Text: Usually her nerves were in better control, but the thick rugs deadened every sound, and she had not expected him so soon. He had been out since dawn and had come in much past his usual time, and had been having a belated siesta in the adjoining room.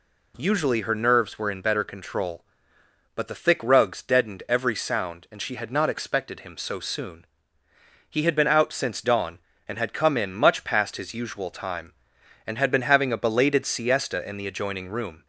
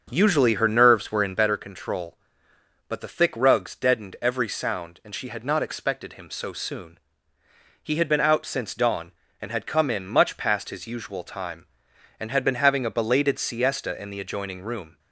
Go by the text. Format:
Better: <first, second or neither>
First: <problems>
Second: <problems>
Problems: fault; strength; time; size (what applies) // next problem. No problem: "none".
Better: first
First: none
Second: starts louder than the rest; until 1.6 s; 6.5 dB